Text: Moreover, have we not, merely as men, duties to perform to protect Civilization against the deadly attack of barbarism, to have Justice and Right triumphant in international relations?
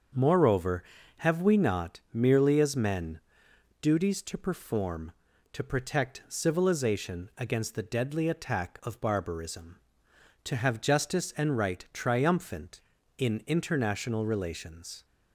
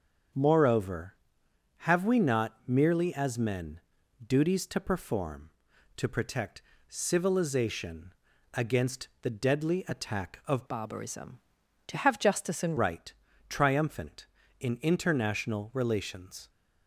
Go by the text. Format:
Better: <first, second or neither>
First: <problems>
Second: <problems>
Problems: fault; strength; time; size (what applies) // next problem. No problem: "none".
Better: first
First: starts louder than the rest; until 1.5 s; 6.5 dB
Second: starts louder than the rest; until 1.9 s; 7 dB // pauses between "protect" and "Civilization"; slight; at 6.6 s; 0.32 s long // pauses between "Civilization" and "against"; at 8.1 s; 0.42 s long // changes voice from "barbarism" to "and"; from 10.6 to 12.7 s; 2.1 s long // pauses between "Right" and "triumphant"; slight; at 13.1 s; 0.34 s long